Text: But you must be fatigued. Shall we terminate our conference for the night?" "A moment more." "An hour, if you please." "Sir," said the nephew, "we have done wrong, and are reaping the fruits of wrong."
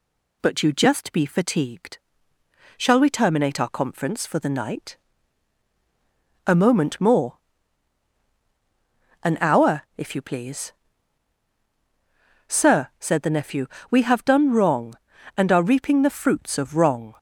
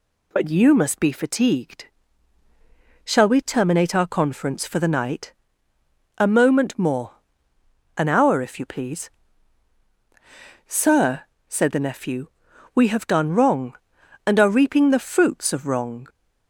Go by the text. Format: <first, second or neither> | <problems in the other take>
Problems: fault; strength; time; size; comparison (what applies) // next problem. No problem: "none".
second | says "just" for "must"; at 0.7 s